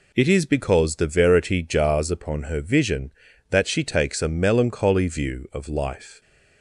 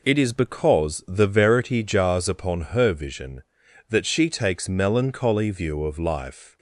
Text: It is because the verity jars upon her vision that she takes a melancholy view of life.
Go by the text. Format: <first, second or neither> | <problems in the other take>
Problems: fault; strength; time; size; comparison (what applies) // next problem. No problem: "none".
first | pauses between "upon" and "her"; slight; at 2.5 s; 0.16 s long // skips "a"; at 4.6 s